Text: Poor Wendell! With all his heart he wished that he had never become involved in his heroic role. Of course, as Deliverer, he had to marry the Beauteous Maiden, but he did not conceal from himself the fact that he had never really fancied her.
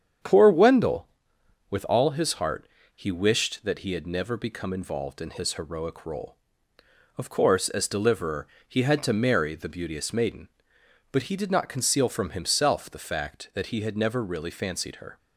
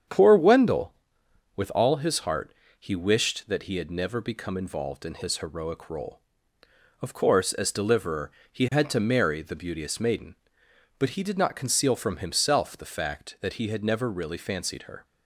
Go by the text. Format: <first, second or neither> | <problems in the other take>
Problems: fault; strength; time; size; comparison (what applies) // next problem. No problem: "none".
neither | starts louder than the rest; strong; the same in both // pauses between "heart" and "he"; slight; the same in both